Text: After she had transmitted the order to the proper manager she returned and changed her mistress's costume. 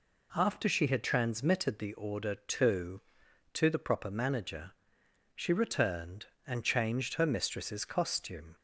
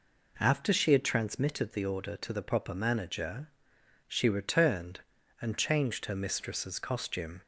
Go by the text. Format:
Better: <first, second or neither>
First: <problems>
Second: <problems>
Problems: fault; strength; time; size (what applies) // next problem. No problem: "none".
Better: second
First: says "to" twice; at 3.5 s // pauses between "manager" and "she"; noticeable; at 4.7 s; 0.64 s long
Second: pauses between "manager" and "she"; noticeable; at 3.4 s; 0.58 s long